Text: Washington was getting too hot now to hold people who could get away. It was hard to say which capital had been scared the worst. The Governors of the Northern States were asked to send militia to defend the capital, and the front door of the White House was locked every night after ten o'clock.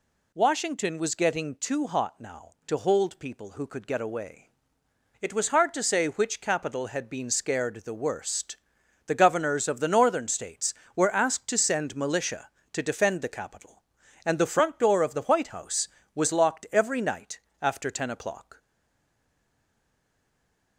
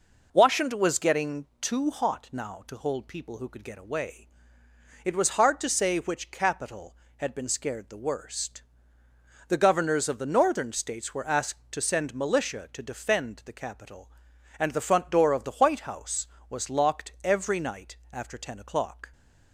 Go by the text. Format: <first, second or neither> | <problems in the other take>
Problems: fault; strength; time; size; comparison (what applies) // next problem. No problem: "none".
second | pauses between "night" and "after"; slight; at 17.4 s; 0.20 s long; slight in the second // stays silent after the last word; from 18.5 s on; 2.2 s long